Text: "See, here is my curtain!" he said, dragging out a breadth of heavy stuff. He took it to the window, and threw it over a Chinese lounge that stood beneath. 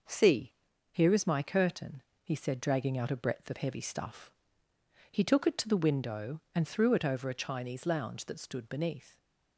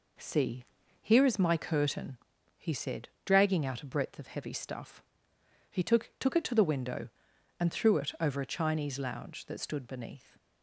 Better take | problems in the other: first | says "took" twice; at 6.1 s

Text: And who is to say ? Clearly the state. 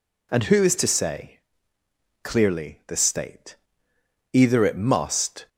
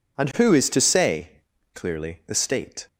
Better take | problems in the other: second | goes on to say "Either it must"; noticeable; from 4.3 s on; 1.1 s long

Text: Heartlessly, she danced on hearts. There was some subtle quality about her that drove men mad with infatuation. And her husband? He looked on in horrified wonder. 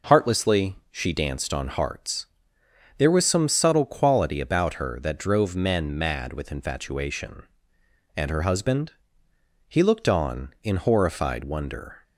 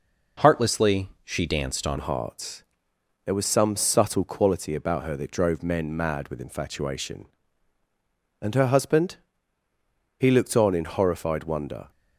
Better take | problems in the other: first | changes voice at "hearts"; from 1.9 s on; 10.0 s long

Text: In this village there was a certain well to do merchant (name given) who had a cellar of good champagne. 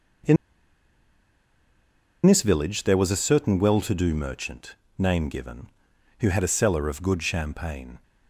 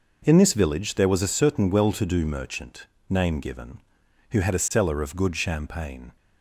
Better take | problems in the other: second | pauses between "In" and "this"; strong; at 0.3 s; 1.9 s long

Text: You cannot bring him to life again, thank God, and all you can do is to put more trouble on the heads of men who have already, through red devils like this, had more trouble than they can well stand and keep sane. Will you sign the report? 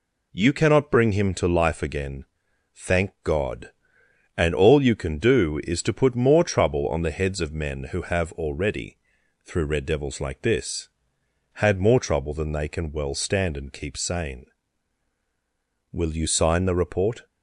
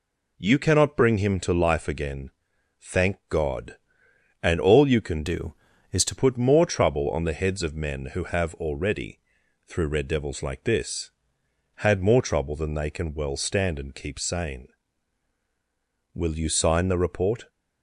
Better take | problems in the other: first | changes voice from "do" to "to"; from 5.2 to 6.1 s; 0.9 s long

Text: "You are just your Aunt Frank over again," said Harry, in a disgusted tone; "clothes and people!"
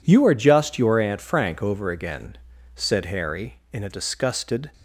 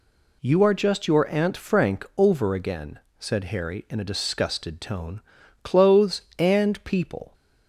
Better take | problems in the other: second | stops before "tone clothes and people"; at 4.7 s

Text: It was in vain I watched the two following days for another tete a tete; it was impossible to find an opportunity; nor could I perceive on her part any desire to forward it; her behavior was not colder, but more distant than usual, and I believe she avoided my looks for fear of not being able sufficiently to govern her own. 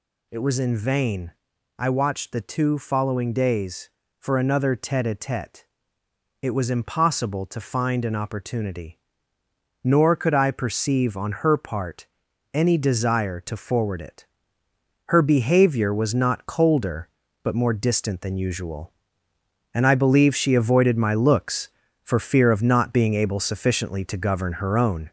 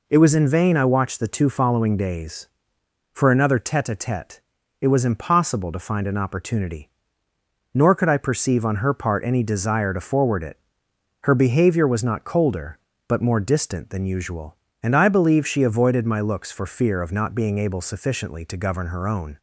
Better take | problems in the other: second | gets louder; noticeable; throughout; 4.5 dB // pauses between "vain" and "I"; noticeable; at 1.3 s; 0.46 s long // pauses between "part" and "any"; noticeable; at 12.0 s; 0.46 s long

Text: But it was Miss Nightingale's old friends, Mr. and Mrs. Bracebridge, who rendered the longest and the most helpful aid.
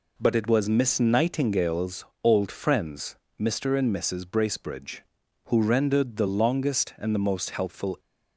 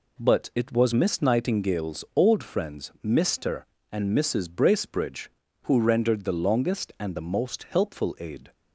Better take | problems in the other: second | pauses between "Nightingale's" and "old"; slight; at 2.0 s; 0.20 s long // stops before "aid"; at 7.9 s

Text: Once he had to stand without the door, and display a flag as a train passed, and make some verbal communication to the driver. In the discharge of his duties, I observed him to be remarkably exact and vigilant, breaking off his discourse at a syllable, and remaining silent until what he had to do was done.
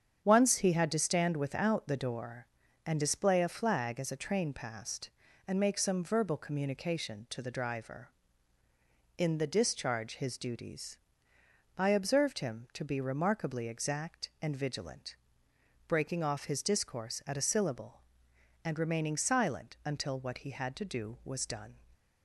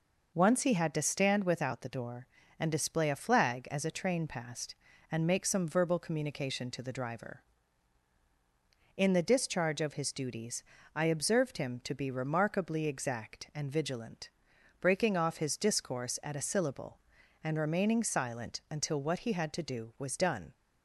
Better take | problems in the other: second | starts louder than the rest; strong; until 1.2 s; 7.5 dB // skips "of"; at 10.1 s

